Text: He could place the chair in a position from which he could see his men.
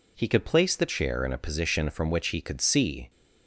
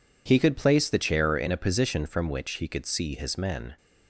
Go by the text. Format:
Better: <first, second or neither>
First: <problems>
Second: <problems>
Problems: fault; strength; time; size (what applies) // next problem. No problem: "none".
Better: second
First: stops before "his men"; at 3.0 s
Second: none